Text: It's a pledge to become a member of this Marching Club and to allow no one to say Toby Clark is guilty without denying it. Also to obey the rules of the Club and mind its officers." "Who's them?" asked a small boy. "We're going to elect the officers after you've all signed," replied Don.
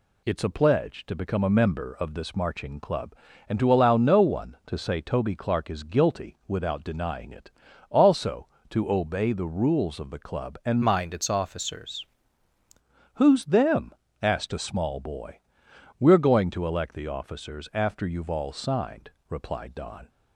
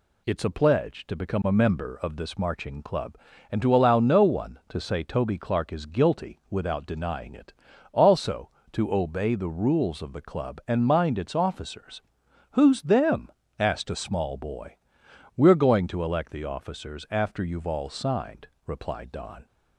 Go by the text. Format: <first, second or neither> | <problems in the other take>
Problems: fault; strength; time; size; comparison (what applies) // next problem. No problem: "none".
second | changes voice from "mind" to "officers"; from 10.8 to 12.0 s; 1.2 s long